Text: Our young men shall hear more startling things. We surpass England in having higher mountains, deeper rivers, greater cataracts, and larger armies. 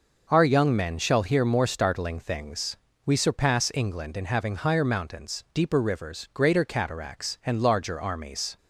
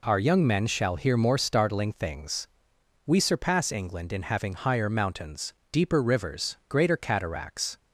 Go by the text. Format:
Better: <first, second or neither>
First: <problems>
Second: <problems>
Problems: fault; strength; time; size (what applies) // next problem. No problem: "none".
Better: first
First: none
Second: stops before "and larger armies"; at 7.7 s